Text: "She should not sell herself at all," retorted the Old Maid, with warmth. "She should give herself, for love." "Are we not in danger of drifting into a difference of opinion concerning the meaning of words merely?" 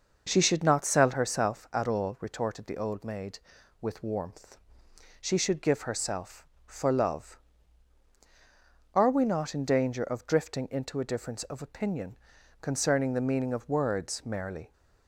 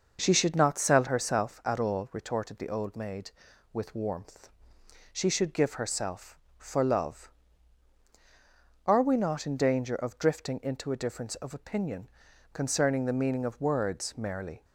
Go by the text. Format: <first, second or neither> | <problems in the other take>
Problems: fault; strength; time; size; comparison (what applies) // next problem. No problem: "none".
neither | pauses between "opinion" and "concerning"; the same in both